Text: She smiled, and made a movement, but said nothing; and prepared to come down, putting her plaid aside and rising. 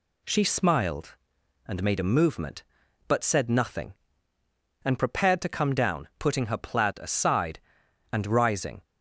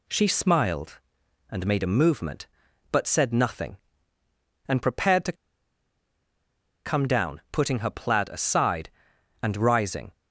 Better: first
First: none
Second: pauses between "to" and "come"; strong; at 5.3 s; 1.5 s long

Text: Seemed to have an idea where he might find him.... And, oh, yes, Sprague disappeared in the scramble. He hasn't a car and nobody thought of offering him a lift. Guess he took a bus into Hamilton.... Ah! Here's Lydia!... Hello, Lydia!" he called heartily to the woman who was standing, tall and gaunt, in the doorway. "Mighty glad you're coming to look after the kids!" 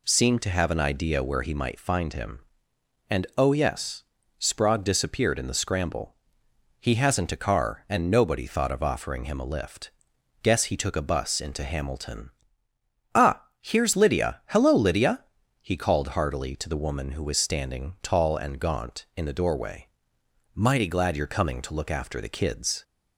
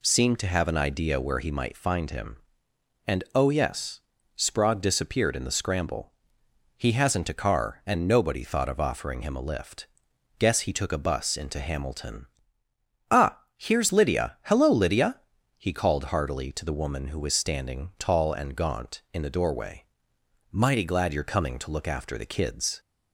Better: neither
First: none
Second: none

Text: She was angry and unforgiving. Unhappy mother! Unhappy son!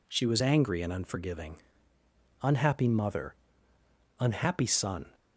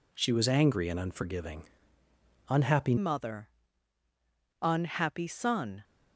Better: first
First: none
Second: changes voice at "mother"; from 2.9 s on; 2.9 s long

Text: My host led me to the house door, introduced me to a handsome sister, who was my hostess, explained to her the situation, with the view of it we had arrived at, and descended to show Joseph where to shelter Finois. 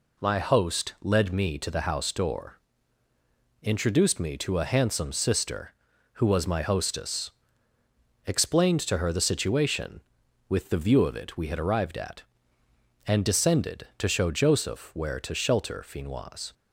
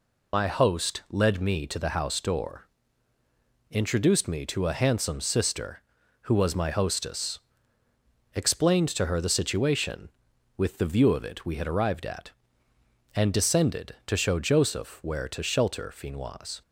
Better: first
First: none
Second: loses the start of "My"; at 0.3 s; 55 ms

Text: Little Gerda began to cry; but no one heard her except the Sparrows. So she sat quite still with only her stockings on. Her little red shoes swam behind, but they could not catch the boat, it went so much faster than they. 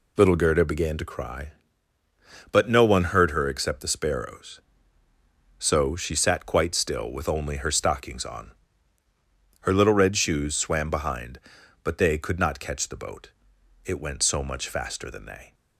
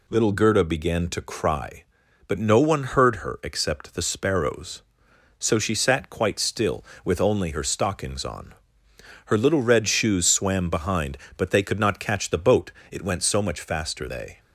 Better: first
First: none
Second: skips "than"; at 14.0 s

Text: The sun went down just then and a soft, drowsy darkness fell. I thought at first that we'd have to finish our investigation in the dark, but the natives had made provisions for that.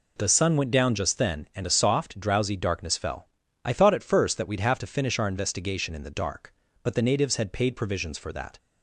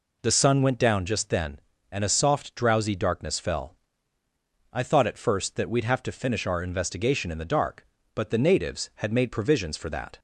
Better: second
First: says "paid" for "made"; at 7.5 s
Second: none

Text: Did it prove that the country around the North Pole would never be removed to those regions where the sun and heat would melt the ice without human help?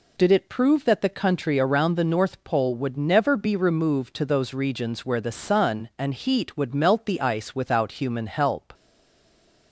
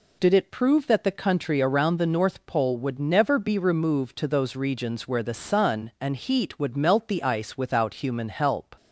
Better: second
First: stays silent after the last word; from 8.7 s on; 1.0 s long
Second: none

